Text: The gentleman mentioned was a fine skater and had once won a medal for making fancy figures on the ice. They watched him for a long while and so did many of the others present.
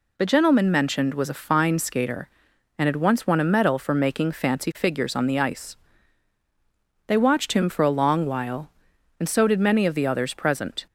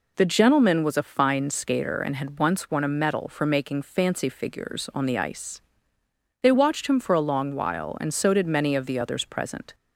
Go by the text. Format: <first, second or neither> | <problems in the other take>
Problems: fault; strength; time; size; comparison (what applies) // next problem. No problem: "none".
first | skips "mentioned"; at 0.8 s